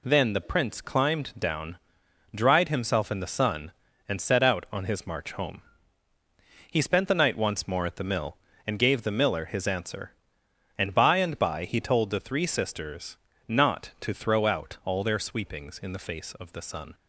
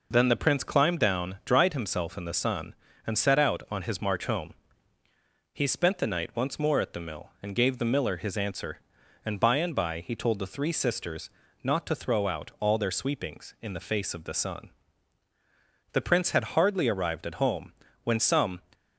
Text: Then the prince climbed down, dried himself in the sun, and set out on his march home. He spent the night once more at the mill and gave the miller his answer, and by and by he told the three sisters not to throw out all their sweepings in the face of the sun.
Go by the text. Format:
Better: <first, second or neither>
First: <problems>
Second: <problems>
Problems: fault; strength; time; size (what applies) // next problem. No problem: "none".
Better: first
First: pauses between "sisters" and "not"; slight; at 13.1 s; 0.32 s long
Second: pauses between "sisters" and "not"; slight; at 11.2 s; 0.34 s long // goes on to say "The prince had hardly arrived at home when some"; strong; from 15.9 s on; 2.6 s long